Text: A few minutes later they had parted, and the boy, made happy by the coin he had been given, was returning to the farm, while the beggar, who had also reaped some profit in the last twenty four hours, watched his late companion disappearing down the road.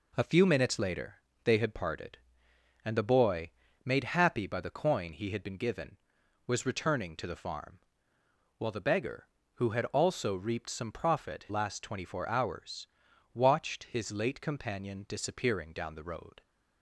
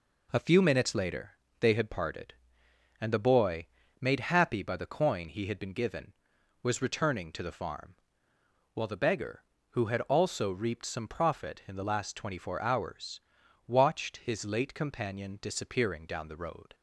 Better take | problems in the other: second | pauses between "later" and "they"; slight; at 1.1 s; 0.28 s long; slight in the second // skips "in the"; at 11.4 s

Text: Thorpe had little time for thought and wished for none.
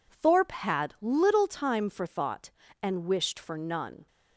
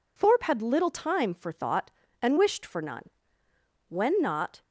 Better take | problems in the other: first | goes on to say "When not"; noticeable; from 3.8 s on; 0.74 s long

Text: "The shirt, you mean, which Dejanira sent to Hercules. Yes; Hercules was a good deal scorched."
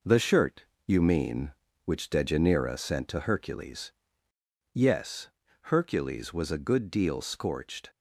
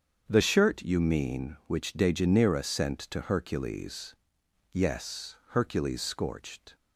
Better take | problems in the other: first | starts louder than the rest; strong; until 1.2 s; 7.5 dB // skips "was a good deal"; at 6.0 s

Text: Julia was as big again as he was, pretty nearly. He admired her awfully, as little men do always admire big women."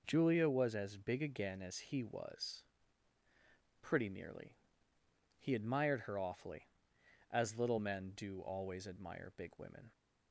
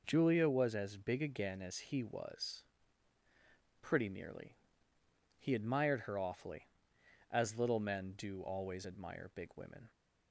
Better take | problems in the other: neither | none

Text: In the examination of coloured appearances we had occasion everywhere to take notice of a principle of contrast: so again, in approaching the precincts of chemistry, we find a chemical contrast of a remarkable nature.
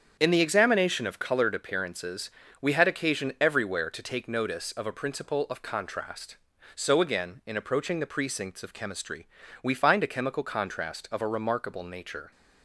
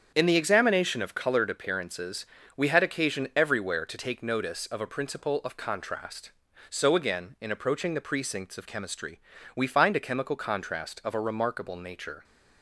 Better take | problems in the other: neither | starts louder than the rest; strong; the same in both // pauses between "appearances" and "we"; slight; the same in both

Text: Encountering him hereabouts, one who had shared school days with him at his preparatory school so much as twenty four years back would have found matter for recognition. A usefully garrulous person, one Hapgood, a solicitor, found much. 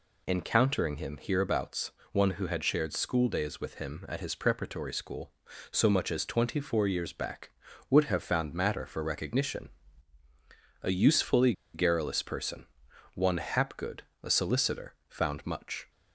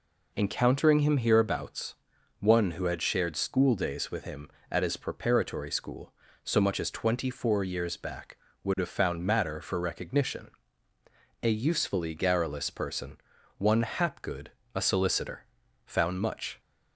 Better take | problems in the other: second | pauses between "usefully" and "garrulous"; slight; at 11.5 s; 0.21 s long

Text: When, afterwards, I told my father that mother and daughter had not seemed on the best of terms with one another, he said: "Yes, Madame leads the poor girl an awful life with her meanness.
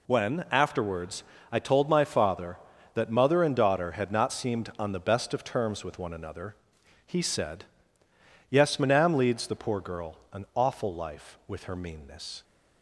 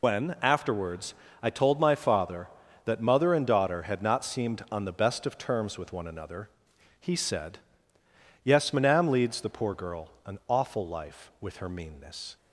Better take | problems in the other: first | loses the start of "When"; at 0.0 s; 65 ms // pauses between "girl" and "an"; slight; at 10.0 s; 0.16 s long; slight in the first

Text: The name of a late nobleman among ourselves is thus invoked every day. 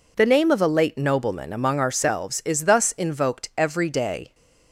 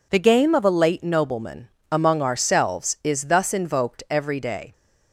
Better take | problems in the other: first | says "game" for "name"; at 0.3 s // pauses between "nobleman" and "among"; slight; at 1.6 s; 0.24 s long

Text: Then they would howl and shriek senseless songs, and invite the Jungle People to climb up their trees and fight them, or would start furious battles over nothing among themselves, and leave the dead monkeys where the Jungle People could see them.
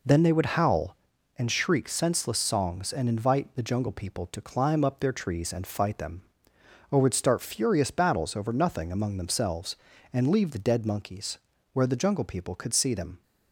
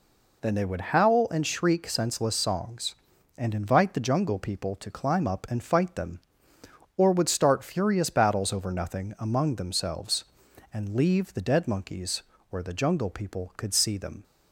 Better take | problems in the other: first | skips "their trees"; at 5.4 s // pauses between "monkeys" and "where"; slight; at 12.2 s; 0.26 s long; slight in the first

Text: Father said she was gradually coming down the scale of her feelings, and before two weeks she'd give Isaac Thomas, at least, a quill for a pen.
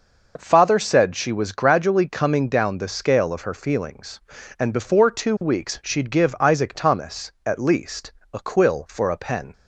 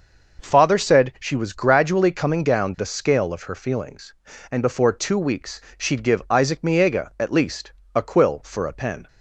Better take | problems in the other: first | pauses between "weeks" and "she'd"; slight; at 5.6 s; 0.16 s long // says "Miega" for "Thomas"; at 6.6 s

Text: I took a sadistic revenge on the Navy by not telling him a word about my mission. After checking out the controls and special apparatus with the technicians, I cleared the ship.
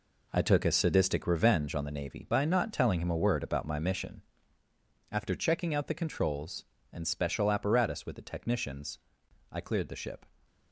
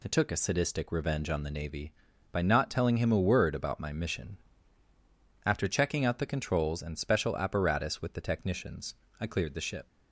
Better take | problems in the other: second | gets quieter; strong; throughout; 9.5 dB

